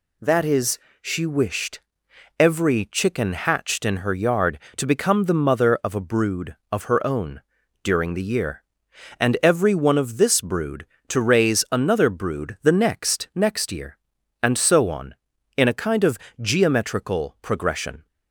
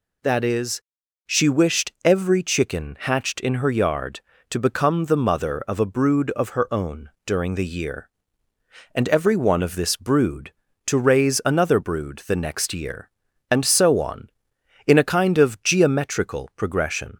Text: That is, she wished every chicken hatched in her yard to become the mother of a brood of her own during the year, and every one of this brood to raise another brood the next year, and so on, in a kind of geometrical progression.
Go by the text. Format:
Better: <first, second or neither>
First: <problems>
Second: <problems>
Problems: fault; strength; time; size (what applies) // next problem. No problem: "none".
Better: second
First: pauses between "wished" and "every"; noticeable; at 1.8 s; 0.58 s long // pauses between "own" and "during"; at 7.4 s; 0.42 s long // says "next" twice; at 13.3 s // pauses between "of" and "geometrical"; slight; at 16.1 s; 0.22 s long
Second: pauses between "own" and "during"; slight; at 7.0 s; 0.16 s long